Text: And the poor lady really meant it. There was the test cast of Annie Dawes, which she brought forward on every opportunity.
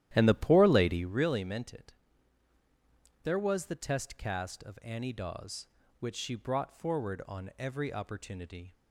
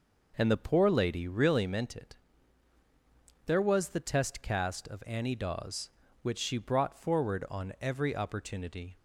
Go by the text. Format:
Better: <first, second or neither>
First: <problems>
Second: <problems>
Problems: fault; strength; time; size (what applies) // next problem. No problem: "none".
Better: second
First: starts louder than the rest; strong; until 1.2 s; 12.5 dB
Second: none